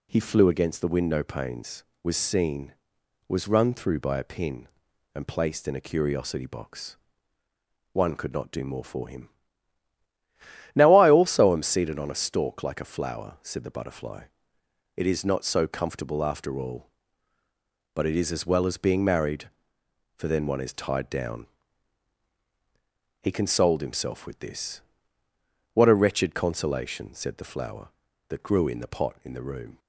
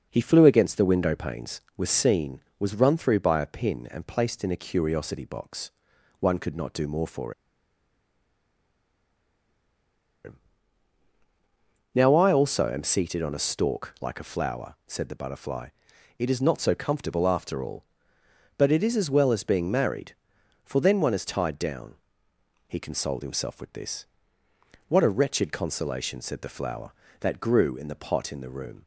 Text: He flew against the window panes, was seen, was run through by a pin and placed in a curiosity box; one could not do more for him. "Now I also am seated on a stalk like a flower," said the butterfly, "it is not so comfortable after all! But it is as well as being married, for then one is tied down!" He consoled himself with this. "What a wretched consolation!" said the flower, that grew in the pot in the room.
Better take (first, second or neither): first